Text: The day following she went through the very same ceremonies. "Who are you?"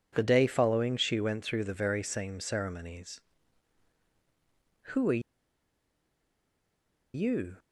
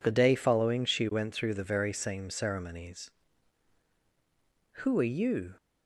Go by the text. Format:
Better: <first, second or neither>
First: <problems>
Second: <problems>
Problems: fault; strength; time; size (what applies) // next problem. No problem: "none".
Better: second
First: pauses between "are" and "you"; strong; at 5.2 s; 1.9 s long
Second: none